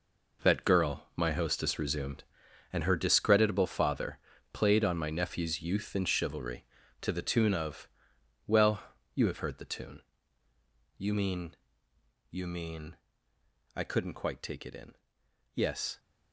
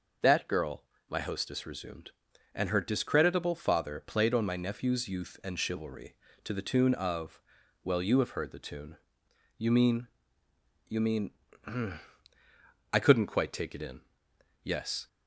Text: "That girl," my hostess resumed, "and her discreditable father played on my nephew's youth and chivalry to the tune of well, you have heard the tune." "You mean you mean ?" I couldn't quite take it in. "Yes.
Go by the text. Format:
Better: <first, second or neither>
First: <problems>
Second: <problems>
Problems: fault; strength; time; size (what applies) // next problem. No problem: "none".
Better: second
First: gets quieter; strong; throughout; 15.5 dB // pauses between "father" and "played"; slight; at 4.1 s; 0.34 s long // pauses between "of" and "well"; noticeable; at 7.8 s; 0.58 s long // pauses between "mean" and "you"; noticeable; at 11.5 s; 0.74 s long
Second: pauses between "of" and "well"; at 7.4 s; 0.42 s long // pauses between "mean" and "you"; noticeable; at 10.0 s; 0.80 s long